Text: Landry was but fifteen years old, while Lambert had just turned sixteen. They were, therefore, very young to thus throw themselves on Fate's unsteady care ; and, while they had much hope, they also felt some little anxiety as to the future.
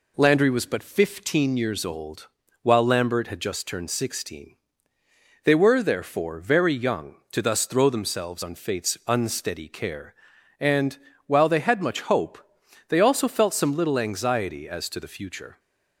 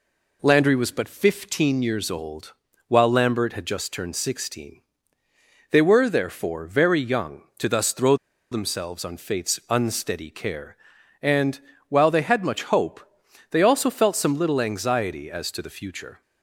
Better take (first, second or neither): first